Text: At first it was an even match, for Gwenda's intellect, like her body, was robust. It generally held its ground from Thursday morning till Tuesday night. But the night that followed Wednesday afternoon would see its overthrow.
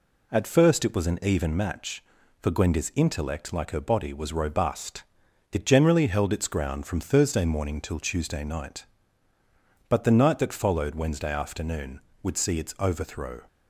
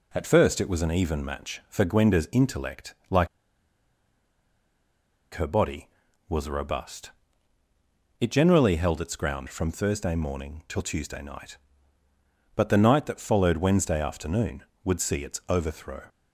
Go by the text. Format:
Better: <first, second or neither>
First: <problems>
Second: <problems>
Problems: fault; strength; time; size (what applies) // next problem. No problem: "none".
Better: first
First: none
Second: pauses between "like" and "her"; strong; at 3.2 s; 2.0 s long